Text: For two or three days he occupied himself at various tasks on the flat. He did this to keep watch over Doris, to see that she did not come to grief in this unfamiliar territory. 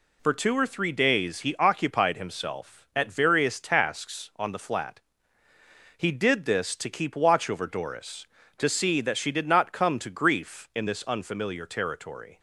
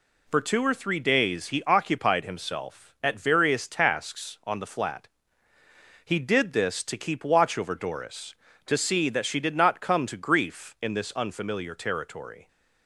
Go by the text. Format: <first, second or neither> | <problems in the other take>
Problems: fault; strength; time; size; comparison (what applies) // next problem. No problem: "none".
neither | none